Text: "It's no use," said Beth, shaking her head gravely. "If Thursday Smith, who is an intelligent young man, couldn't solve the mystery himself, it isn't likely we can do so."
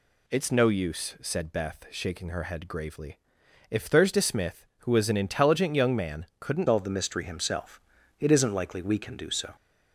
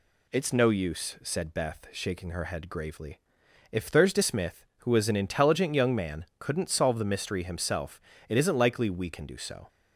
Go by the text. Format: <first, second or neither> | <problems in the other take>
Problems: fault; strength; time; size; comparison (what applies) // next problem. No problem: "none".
second | changes voice at "solve"; from 6.6 s on; 2.9 s long